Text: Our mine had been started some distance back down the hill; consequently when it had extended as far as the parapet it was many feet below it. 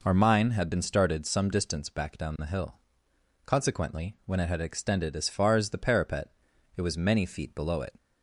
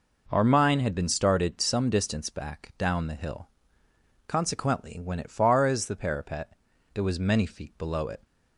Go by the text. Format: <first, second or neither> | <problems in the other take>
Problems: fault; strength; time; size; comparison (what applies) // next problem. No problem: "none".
first | skips "had extended as"; at 5.3 s // pauses between "parapet" and "it"; at 6.5 s; 0.44 s long; noticeable in the first